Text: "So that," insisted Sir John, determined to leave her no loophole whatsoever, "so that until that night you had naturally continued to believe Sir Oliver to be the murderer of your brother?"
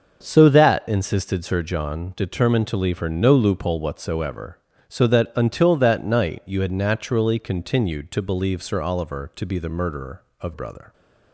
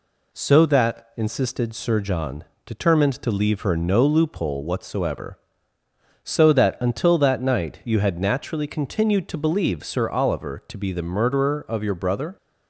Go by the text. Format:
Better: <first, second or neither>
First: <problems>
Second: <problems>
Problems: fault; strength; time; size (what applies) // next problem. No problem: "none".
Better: second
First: starts louder than the rest; until 1.2 s; 6.5 dB // skips "your"; at 10.5 s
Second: none